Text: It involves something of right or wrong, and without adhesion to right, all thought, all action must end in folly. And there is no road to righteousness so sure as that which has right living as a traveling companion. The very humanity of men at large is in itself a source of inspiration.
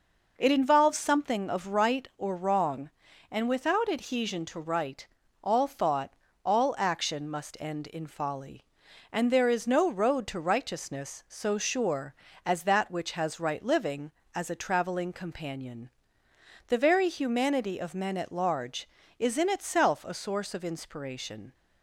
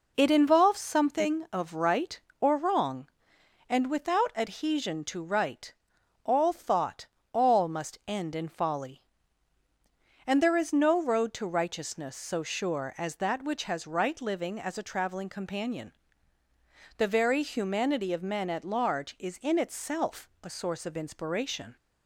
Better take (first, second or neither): first